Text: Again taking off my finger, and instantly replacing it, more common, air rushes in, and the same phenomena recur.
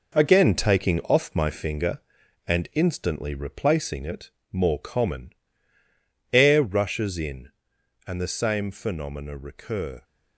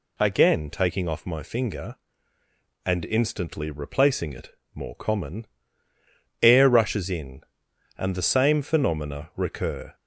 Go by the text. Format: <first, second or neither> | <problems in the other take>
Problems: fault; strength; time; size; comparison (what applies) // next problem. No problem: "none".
second | gets quieter; strong; throughout; 7.5 dB